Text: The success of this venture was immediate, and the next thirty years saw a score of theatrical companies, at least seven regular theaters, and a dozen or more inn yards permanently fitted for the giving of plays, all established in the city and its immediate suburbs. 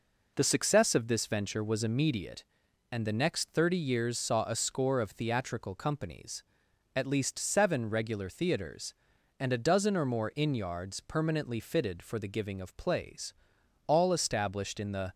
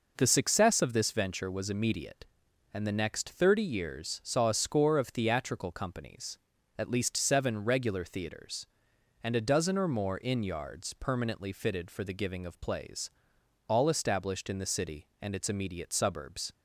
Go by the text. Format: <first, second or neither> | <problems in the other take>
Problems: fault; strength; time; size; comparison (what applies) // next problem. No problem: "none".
second | stops before "city and its immediate suburbs"; at 15.1 s